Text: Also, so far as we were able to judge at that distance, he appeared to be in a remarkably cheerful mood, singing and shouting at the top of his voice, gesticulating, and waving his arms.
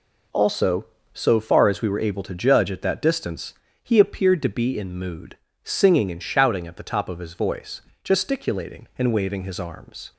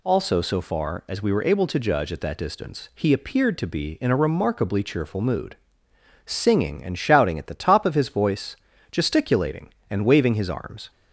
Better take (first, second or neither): second